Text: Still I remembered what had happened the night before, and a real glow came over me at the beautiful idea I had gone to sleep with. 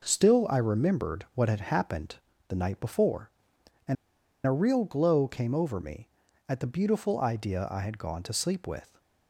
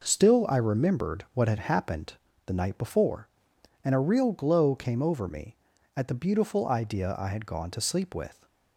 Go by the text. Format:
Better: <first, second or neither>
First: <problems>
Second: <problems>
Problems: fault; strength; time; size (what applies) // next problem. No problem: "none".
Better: second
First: pauses between "happened" and "the"; slight; at 2.1 s; 0.32 s long // pauses between "and" and "a"; noticeable; at 3.9 s; 0.50 s long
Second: pauses between "happened" and "the"; slight; at 2.1 s; 0.32 s long